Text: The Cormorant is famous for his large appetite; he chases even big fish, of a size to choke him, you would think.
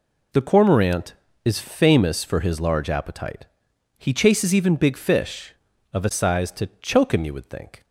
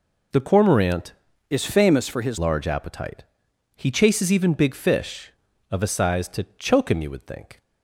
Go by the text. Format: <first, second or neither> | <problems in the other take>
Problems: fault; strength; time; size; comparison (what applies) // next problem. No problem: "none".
first | changes voice from "is" to "his"; from 1.4 to 2.3 s; 0.9 s long